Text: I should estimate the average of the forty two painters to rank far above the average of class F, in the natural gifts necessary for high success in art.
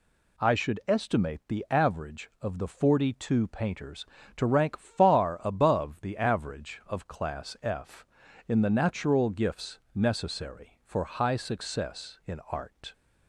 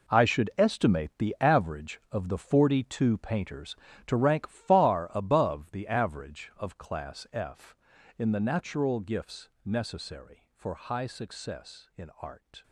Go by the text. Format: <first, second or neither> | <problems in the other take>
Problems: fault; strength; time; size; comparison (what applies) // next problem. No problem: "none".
first | gets quieter; strong; throughout; 14 dB // pauses between "gifts" and "necessary"; slight; at 9.4 s; 0.16 s long; slight in the first